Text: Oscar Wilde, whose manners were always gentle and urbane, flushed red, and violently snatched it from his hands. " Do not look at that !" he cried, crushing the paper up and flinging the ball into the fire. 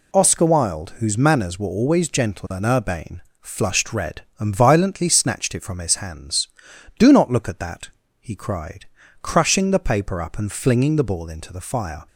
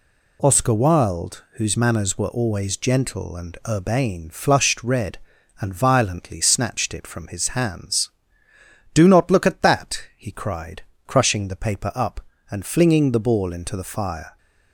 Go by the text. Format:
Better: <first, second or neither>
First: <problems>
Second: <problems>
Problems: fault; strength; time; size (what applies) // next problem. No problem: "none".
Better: neither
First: none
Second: none